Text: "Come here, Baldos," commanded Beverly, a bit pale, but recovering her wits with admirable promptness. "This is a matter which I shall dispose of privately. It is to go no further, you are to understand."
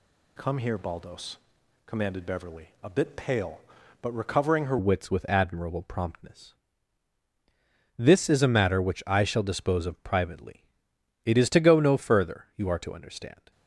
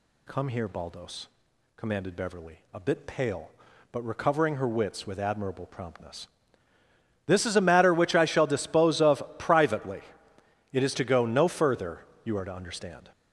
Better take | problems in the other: second | changes voice at "wits"; from 4.7 s on; 8.8 s long

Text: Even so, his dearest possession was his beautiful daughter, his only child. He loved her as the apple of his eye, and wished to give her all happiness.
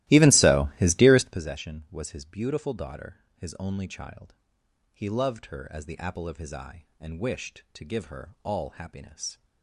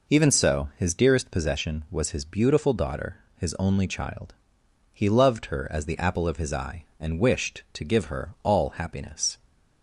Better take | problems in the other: second | starts louder than the rest; strong; until 1.4 s; 16.5 dB

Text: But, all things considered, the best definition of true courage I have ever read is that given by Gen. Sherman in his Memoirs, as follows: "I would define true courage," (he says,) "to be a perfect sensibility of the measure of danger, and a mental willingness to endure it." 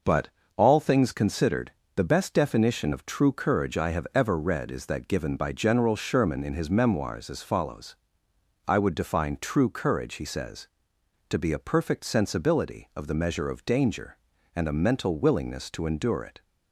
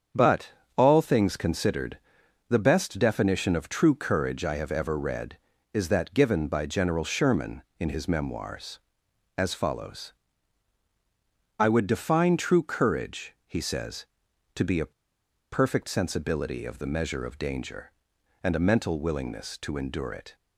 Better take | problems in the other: first | starts louder than the rest; strong; until 1.3 s; 7.5 dB // pauses between "a" and "perfect"; noticeable; at 14.9 s; 0.62 s long

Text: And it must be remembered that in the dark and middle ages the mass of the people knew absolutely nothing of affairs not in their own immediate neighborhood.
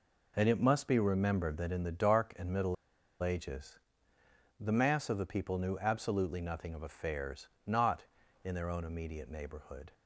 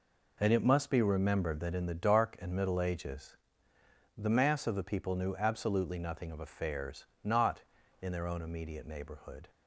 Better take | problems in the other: second | pauses between "middle" and "ages"; noticeable; at 2.7 s; 0.46 s long // pauses between "ages" and "the"; noticeable; at 3.7 s; 0.80 s long; noticeable in the second // pauses between "affairs" and "not"; slight; at 7.4 s; 0.18 s long; slight in the second

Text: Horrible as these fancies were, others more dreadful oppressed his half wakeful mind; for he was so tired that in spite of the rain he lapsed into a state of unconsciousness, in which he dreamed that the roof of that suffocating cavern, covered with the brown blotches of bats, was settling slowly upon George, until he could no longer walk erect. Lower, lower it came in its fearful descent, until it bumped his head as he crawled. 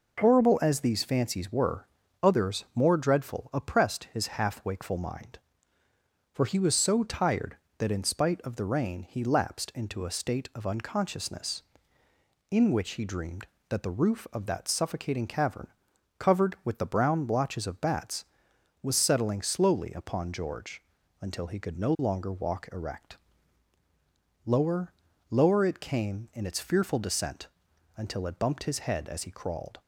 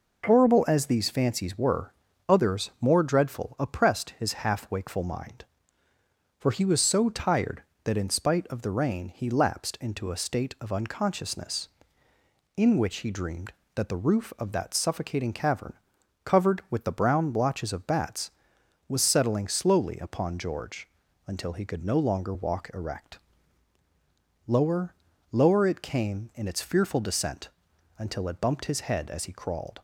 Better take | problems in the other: neither | none

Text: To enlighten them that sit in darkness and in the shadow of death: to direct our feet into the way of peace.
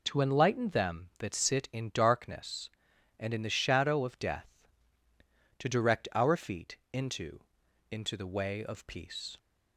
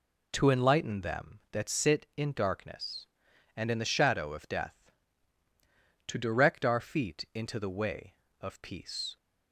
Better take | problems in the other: second | pauses between "feet" and "into"; slight; at 6.7 s; 0.16 s long // says "into" twice; at 7.9 s

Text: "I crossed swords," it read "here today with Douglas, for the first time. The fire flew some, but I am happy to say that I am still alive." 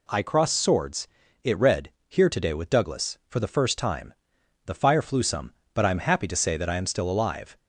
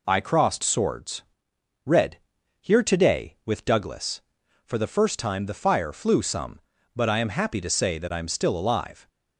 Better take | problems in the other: first | skips "it"; at 1.5 s // pauses between "read" and "here"; at 2.1 s; 0.42 s long; slight in the first

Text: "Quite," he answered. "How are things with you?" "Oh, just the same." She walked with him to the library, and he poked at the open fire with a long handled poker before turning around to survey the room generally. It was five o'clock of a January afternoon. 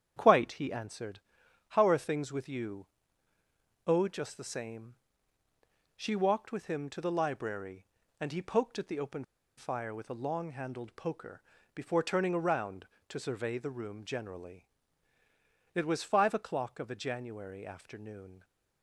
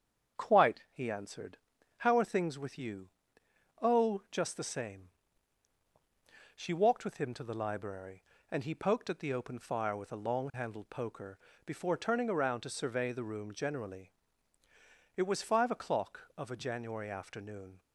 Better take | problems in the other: second | starts louder than the rest; strong; until 1.1 s; 9 dB; strong in the second // pauses between "open" and "fire"; slight; at 9.2 s; 0.34 s long // pauses between "poker" and "before"; slight; at 11.3 s; 0.36 s long; slight in the second

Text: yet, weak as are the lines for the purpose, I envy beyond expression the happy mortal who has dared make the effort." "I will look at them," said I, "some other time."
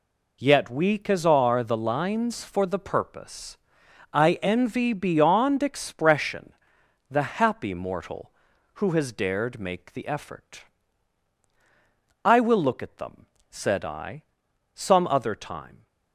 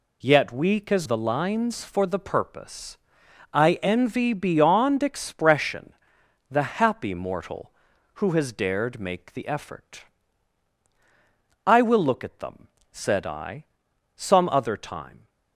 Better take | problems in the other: first | skips "are"; at 1.0 s // pauses between "expression" and "the"; noticeable; at 5.9 s; 0.58 s long; noticeable in the first

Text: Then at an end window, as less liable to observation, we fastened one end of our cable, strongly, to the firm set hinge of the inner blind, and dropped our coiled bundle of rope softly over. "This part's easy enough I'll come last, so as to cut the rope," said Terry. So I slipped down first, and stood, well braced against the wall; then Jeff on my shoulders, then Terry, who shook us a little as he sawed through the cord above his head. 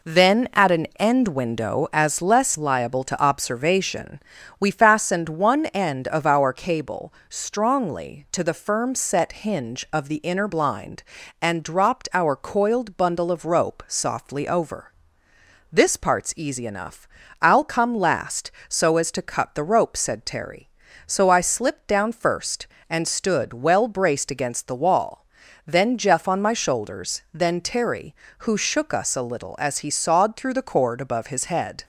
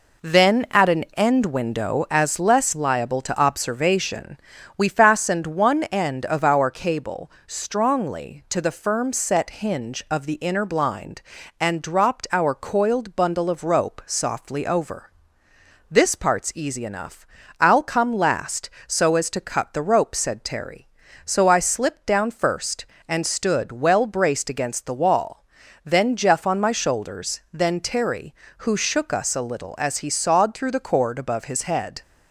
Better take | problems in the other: neither | pauses between "enough" and "I'll"; slight; the same in both

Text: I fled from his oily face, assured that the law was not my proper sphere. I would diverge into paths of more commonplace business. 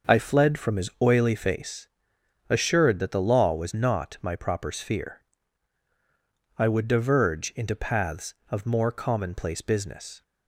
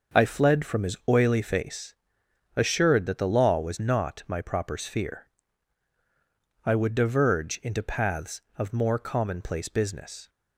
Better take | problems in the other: neither | starts louder than the rest; the same in both

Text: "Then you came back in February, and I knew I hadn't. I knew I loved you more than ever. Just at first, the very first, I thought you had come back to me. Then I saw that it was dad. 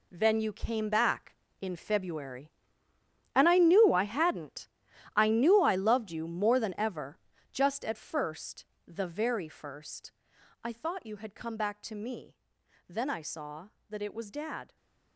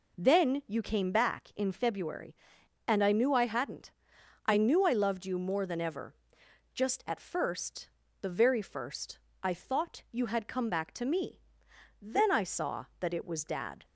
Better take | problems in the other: second | gets quieter; strong; throughout; 10.5 dB

